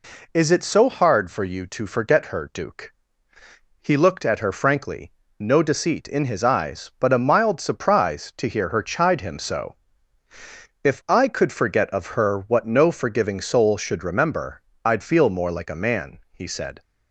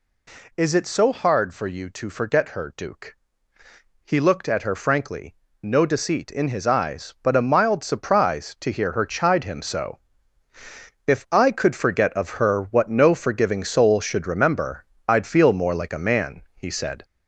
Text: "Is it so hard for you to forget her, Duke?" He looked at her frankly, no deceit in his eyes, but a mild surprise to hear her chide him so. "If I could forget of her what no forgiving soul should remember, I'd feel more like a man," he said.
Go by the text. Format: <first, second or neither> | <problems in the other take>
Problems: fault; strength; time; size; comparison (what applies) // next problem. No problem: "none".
first | gets louder; noticeable; throughout; 4 dB